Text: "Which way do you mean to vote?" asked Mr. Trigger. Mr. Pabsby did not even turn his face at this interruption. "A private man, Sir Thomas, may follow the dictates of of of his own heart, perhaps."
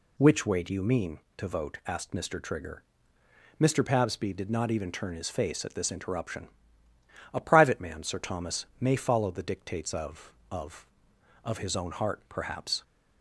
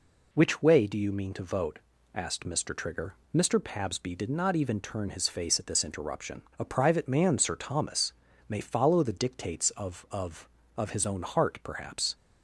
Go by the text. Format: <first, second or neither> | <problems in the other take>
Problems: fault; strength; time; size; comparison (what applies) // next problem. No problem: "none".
neither | none